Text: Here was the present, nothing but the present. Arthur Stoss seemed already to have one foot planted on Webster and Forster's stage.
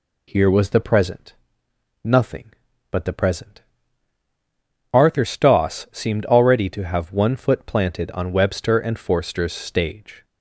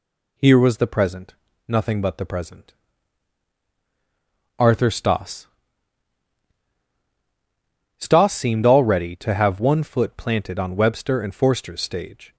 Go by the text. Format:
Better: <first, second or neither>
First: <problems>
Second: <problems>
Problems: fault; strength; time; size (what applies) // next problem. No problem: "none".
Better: first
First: none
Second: says "Stoss" twice; at 7.9 s